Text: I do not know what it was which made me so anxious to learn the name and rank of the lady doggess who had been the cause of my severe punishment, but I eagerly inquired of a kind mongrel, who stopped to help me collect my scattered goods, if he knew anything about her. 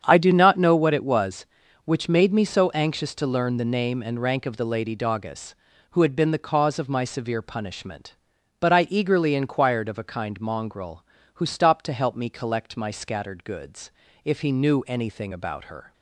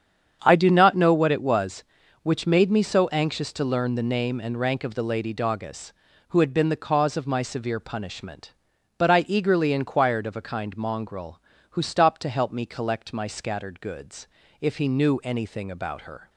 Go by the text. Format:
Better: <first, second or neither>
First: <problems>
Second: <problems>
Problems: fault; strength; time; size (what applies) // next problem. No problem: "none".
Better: neither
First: starts louder than the rest; strong; until 1.0 s; 8 dB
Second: starts louder than the rest; strong; until 1.4 s; 8 dB